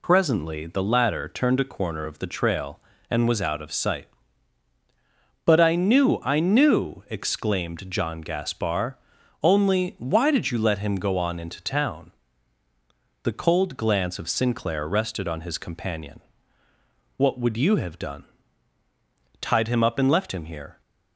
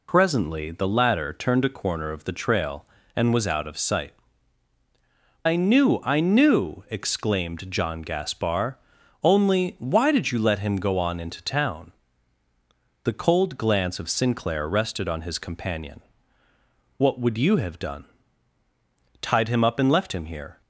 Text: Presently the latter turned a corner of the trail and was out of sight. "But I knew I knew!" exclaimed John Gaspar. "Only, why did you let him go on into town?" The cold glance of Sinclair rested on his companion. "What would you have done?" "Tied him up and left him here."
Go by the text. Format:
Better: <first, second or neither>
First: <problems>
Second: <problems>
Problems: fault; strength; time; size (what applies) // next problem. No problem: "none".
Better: first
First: none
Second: skips "But"; at 4.7 s